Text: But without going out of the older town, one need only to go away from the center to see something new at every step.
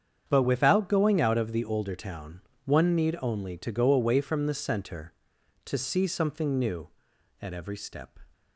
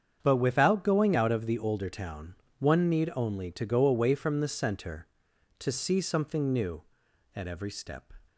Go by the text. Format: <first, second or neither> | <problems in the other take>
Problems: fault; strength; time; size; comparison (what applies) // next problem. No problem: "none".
neither | starts louder than the rest; strong; the same in both